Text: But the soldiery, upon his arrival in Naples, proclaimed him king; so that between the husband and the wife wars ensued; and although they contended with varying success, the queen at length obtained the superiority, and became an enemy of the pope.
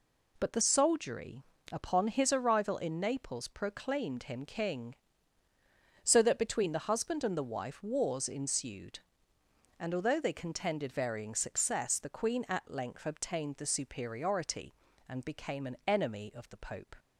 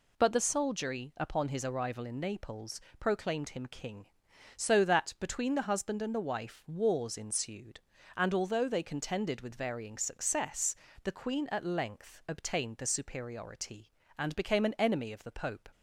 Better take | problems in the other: second | skips "with"; at 10.9 s

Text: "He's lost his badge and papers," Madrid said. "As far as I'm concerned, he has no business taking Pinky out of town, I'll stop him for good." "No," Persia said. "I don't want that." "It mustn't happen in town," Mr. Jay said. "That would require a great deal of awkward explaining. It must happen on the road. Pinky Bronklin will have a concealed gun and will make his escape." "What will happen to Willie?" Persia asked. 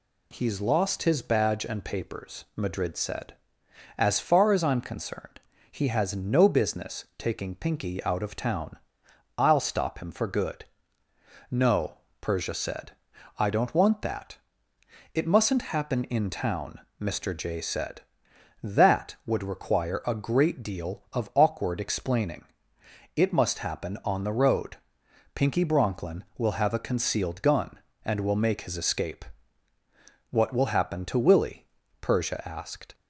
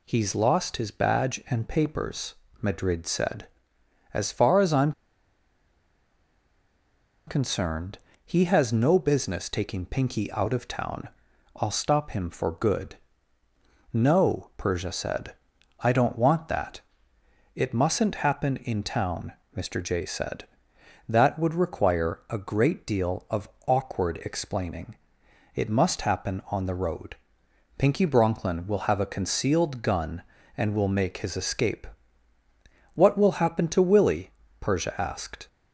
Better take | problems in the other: first | pauses between "I'm" and "concerned"; strong; at 4.9 s; 2.3 s long // pauses between "of" and "awkward"; slight; at 23.4 s; 0.16 s long

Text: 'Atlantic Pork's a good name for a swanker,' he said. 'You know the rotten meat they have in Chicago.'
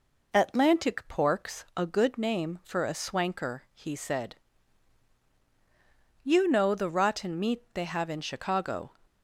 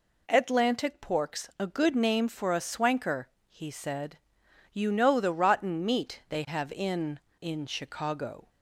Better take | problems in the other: first | says "in" twice; at 7.4 s

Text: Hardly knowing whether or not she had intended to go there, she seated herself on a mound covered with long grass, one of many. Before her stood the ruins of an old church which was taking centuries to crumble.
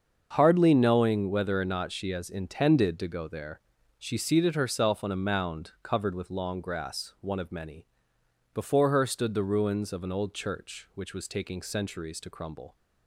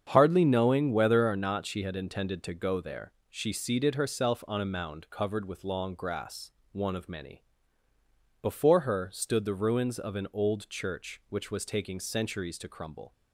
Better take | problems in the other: second | starts louder than the rest; until 1.3 s; 6.5 dB; strong in the second // says "has" for "had"; at 2.1 s

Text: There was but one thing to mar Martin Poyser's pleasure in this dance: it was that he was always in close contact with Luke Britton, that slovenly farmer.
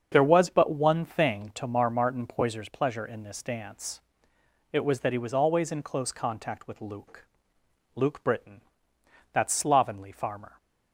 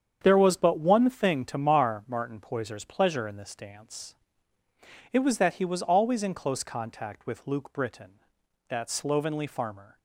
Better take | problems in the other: second | starts louder than the rest; until 1.1 s; 7 dB; strong in the second // says "Luke" twice; at 7.9 s

